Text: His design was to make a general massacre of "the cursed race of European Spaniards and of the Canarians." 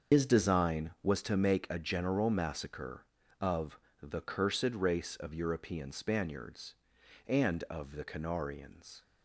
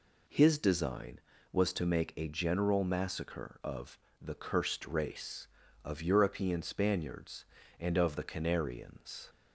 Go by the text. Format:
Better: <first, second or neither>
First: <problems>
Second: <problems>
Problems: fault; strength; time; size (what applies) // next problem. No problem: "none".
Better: second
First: loses the start of "His"; at 0.1 s; 105 ms // starts louder than the rest; until 1.1 s; 6.5 dB // pauses between "of" and "the"; slight; at 3.7 s; 0.24 s long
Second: pauses between "of" and "the"; slight; at 3.9 s; 0.24 s long